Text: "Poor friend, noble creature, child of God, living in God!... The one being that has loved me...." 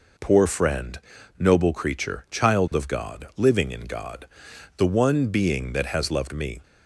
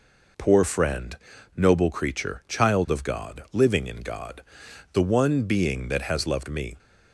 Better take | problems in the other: neither | none

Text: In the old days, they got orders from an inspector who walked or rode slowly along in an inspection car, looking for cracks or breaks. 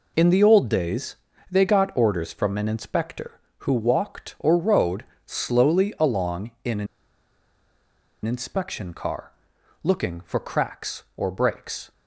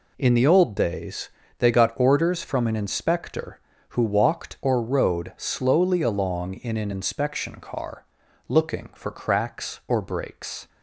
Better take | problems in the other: second | pauses between "rode" and "slowly"; slight; at 5.0 s; 0.22 s long // pauses between "an" and "inspection"; strong; at 6.8 s; 1.3 s long

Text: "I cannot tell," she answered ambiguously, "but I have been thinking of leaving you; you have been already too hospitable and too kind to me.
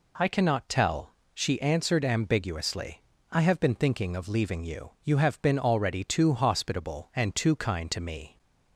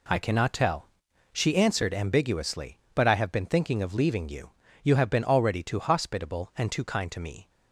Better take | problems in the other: second | skips "but"; at 3.1 s

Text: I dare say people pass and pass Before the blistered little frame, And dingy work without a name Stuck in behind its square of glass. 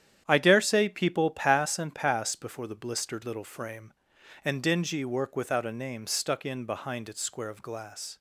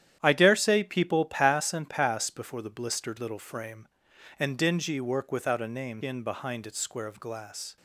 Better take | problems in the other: first | starts louder than the rest; strong; until 1.2 s; 10.5 dB; strong in the first // skips "Stuck"; at 6.0 s

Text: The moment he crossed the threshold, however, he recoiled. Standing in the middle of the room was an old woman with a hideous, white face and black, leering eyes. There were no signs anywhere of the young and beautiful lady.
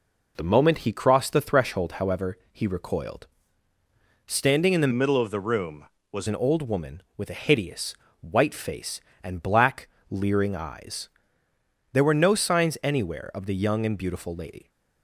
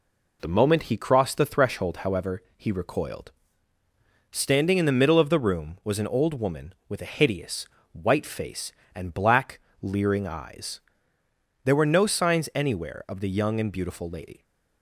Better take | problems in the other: second | changes voice from "middle" to "was"; from 4.9 to 6.2 s; 1.3 s long

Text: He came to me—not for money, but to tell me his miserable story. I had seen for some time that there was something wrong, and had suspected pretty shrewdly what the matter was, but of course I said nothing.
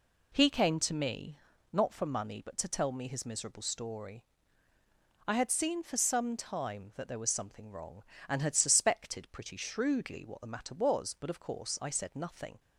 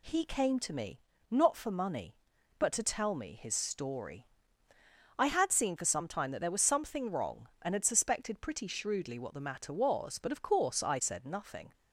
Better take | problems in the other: first | skips "miserable"; at 3.5 s

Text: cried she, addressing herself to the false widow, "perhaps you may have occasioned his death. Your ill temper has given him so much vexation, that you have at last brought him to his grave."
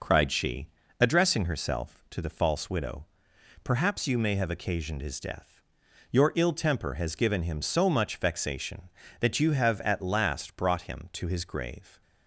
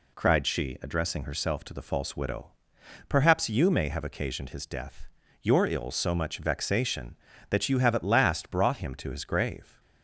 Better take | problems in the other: first | skips "temper has given him"; at 5.8 s

